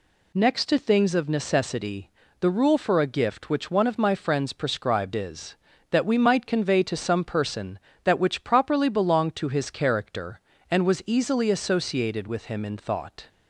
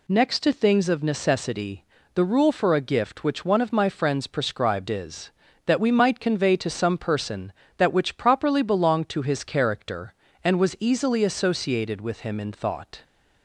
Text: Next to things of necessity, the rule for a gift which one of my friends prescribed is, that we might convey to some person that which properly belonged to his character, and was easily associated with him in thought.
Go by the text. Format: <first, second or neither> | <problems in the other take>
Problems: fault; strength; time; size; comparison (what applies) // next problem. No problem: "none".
neither | none